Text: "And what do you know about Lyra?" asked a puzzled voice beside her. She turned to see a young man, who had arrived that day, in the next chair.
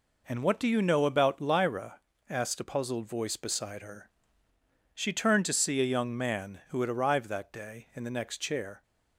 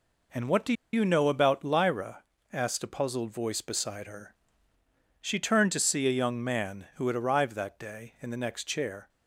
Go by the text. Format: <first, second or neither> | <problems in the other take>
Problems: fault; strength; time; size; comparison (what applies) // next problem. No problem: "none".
first | pauses between "do" and "you"; slight; at 0.7 s; 0.20 s long